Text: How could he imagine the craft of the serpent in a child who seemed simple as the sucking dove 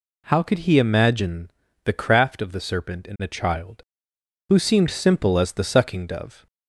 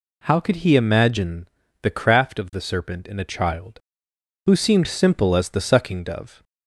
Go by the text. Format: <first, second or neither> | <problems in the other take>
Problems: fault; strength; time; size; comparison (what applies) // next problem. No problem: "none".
neither | pauses between "imagine" and "the"; slight; the same in both